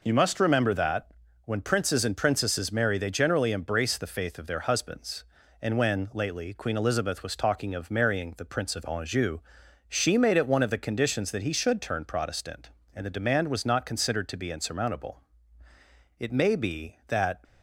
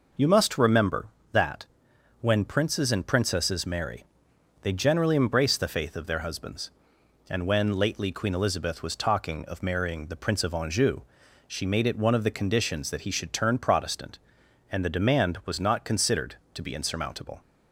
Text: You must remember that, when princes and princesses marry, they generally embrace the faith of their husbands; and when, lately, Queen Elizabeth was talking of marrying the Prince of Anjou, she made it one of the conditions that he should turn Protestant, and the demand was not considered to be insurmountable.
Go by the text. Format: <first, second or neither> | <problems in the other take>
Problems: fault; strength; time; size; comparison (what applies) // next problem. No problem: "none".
second | goes on to say "It may be that"; noticeable; from 16.2 s on; 1.2 s long